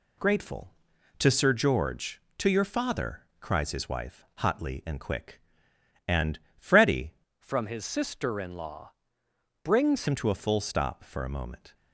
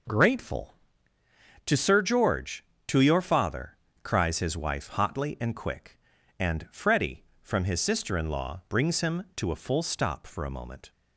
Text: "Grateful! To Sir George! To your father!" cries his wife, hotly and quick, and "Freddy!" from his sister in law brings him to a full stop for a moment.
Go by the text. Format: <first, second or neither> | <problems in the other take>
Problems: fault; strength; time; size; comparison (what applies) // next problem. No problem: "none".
second | pauses between "and" and "Freddy"; slight; at 6.3 s; 0.18 s long // changes voice from "from" to "brings"; from 7.3 to 10.0 s; 2.7 s long // pauses between "law" and "brings"; noticeable; at 8.9 s; 0.70 s long